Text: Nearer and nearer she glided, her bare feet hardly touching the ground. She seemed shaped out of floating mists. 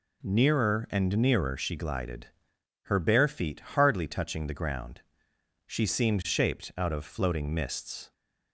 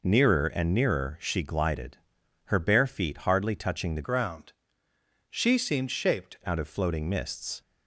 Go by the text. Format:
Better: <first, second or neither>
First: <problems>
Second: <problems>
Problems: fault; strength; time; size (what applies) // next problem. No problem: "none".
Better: first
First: none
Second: changes voice from "ground" to "shaped"; from 4.0 to 6.3 s; 2.3 s long